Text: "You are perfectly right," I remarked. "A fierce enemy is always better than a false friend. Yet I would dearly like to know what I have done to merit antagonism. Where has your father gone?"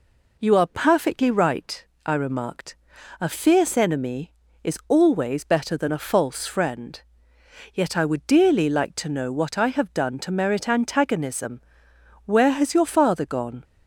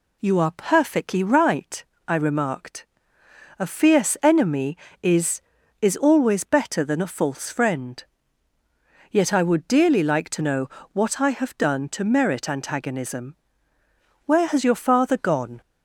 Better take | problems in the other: first | says "is" twice; at 5.8 s // pauses between "know" and "what"; slight; at 10.6 s; 0.24 s long

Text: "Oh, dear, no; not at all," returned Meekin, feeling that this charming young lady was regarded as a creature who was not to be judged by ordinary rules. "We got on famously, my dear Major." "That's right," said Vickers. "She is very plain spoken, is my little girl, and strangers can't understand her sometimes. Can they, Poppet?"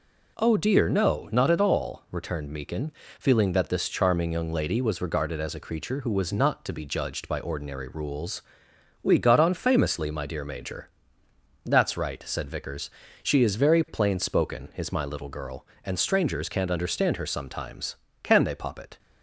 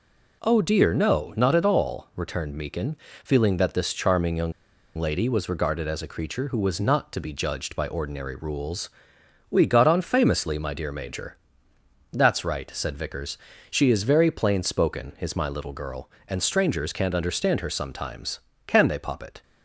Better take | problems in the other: first | pauses between "young" and "lady"; at 4.5 s; 0.45 s long

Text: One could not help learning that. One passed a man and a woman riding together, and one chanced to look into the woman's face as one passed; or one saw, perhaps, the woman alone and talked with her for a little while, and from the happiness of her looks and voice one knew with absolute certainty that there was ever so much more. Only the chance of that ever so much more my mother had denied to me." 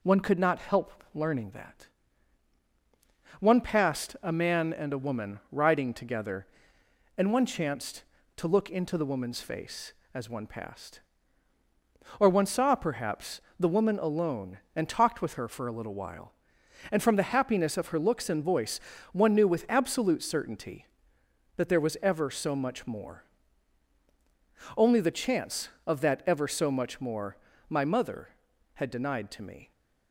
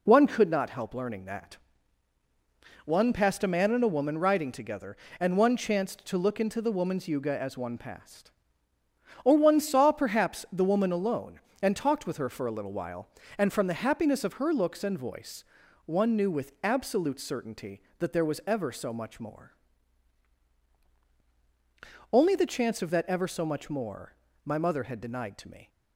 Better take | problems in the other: first | says "yuga" for "face"; at 7.0 s // pauses between "voice" and "one"; at 15.4 s; 0.44 s long; slight in the first // pauses between "more" and "my"; slight; at 24.1 s; 0.30 s long; slight in the first

